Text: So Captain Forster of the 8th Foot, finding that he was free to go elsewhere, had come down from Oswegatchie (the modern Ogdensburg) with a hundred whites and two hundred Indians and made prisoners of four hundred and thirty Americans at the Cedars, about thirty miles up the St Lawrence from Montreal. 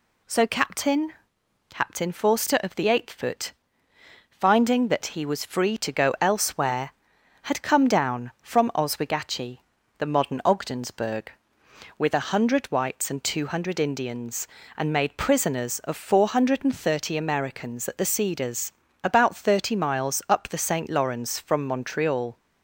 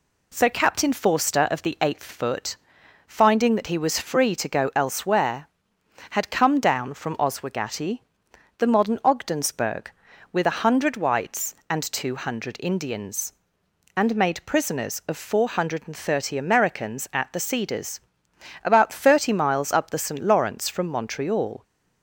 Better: second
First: says "Captain" twice; at 1.6 s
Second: none

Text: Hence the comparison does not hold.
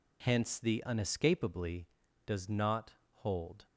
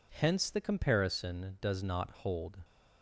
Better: second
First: says "unescapably" for "comparison"; at 0.8 s // pauses between "not" and "hold"; slight; at 2.9 s; 0.16 s long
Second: none

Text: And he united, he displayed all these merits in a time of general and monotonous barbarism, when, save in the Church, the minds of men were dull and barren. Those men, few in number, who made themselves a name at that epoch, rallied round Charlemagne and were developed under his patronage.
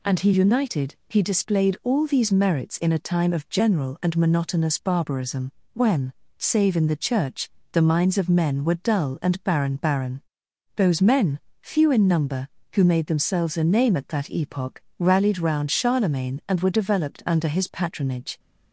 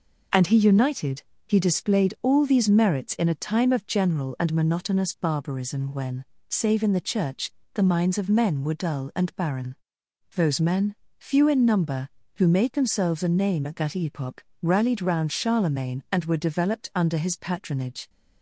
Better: second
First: says "barren" twice; at 9.7 s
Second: none

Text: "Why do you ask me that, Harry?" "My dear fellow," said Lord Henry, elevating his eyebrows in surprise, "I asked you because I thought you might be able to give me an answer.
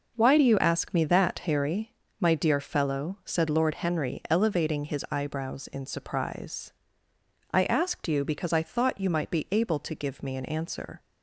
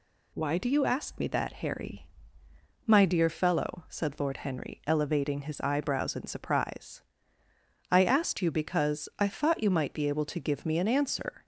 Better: neither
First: none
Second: none

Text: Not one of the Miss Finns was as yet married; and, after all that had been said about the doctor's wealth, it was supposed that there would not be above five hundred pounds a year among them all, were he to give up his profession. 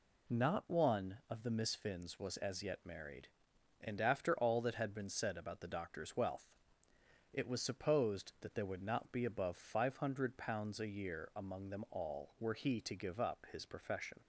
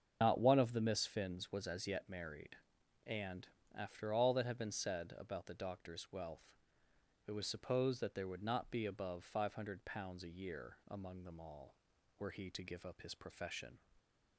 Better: first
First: none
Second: loses the start of "Not"; at 0.2 s; 100 ms // starts louder than the rest; strong; until 1.2 s; 7.5 dB

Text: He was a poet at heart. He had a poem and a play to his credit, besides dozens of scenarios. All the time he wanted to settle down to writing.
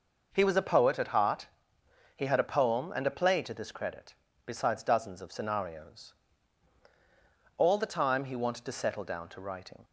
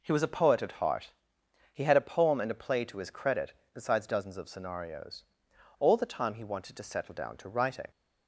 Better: second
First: says "this" for "his"; at 3.5 s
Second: none

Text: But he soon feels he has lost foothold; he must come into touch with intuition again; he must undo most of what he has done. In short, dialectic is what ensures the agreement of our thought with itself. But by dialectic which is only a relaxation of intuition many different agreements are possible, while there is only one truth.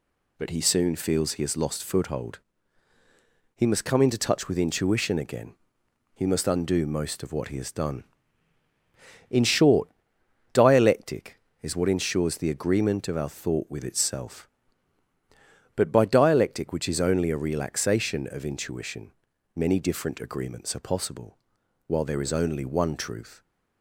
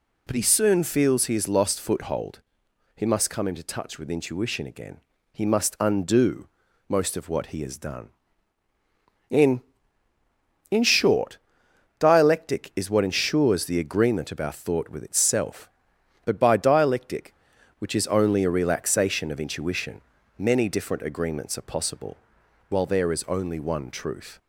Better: first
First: pauses between "intuition" and "many"; at 19.1 s; 0.44 s long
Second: pauses between "undo" and "most"; at 6.4 s; 0.42 s long // says "In" twice; at 10.6 s // pauses between "intuition" and "many"; at 19.9 s; 0.38 s long

